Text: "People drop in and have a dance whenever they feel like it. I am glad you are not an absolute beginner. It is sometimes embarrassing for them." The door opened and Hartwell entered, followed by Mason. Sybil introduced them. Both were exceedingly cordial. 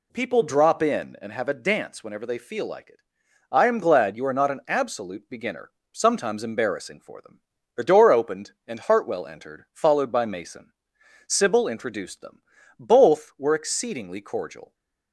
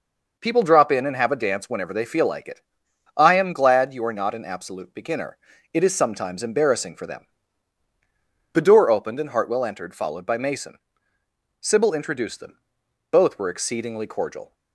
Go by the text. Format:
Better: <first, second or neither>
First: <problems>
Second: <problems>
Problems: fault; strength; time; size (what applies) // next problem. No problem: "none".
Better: second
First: skips "It is"; at 5.8 s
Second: none